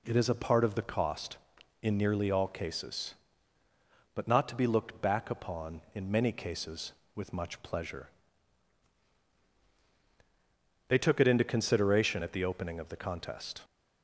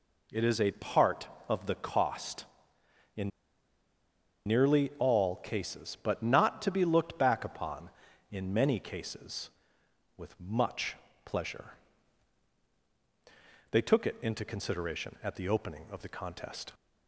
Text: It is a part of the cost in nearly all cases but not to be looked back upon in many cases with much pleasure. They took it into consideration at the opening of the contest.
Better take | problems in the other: first | pauses between "in" and "nearly"; at 3.3 s; 1.1 s long // pauses between "much" and "pleasure"; slight; at 10.9 s; 0.28 s long

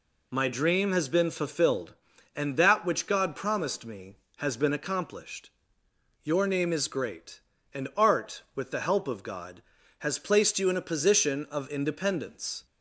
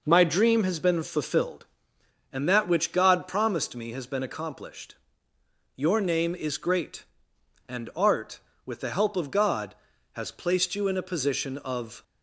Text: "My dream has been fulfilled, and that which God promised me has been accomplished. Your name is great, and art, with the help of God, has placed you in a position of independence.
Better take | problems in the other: first | stops before "independence"; at 12.0 s

